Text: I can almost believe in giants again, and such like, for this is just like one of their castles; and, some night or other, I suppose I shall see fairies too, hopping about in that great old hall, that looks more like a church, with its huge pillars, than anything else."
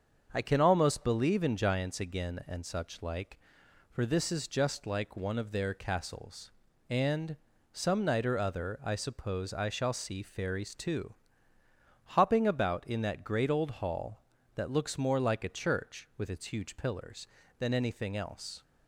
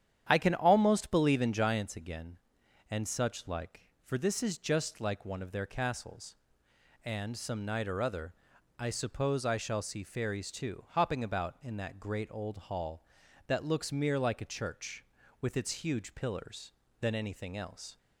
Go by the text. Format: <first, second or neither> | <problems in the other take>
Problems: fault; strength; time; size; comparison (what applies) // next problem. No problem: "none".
first | starts louder than the rest; strong; until 1.3 s; 9.5 dB; also in the first // says "mere" for "more"; at 13.8 s